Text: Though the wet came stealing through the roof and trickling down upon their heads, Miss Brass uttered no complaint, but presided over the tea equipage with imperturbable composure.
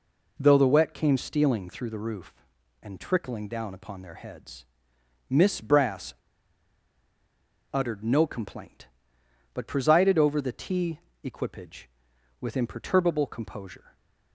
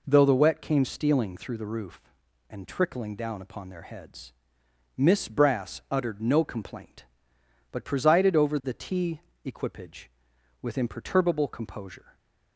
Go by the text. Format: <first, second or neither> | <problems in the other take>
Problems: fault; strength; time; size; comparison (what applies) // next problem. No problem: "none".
second | pauses between "Brass" and "uttered"; strong; at 6.1 s; 1.5 s long // pauses between "tea" and "equipage"; slight; at 10.9 s; 0.24 s long; slight in the second